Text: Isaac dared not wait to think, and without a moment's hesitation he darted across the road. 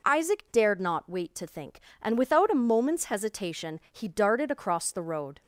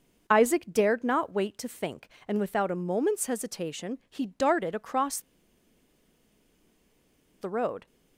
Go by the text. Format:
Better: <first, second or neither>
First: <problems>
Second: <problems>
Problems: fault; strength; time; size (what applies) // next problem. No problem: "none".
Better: first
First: none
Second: pauses between "across" and "the"; strong; at 5.2 s; 2.2 s long